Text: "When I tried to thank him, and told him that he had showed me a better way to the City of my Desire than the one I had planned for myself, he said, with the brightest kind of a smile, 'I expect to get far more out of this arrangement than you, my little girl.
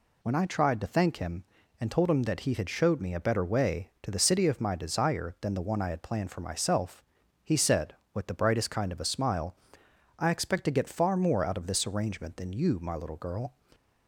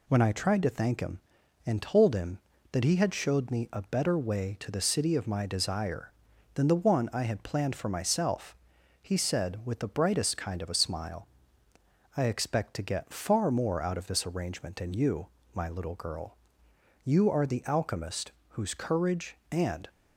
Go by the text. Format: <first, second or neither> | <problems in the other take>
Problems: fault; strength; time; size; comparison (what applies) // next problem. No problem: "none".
first | goes on to say "You are the alchemist whose courage and"; strong; from 17.0 s on; 2.8 s long